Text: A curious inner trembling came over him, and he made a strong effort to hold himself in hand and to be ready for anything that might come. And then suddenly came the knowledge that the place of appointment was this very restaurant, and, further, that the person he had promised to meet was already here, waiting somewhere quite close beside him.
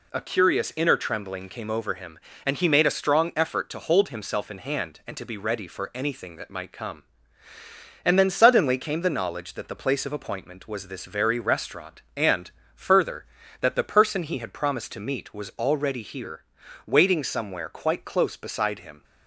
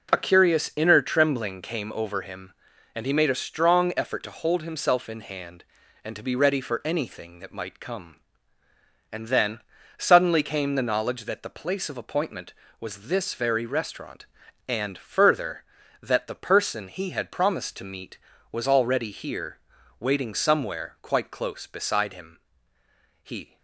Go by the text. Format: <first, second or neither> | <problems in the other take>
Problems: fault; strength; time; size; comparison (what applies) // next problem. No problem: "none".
first | pauses between "then" and "suddenly"; at 9.5 s; 0.40 s long // goes on to say "He"; slight; from 23.2 s on; 0.36 s long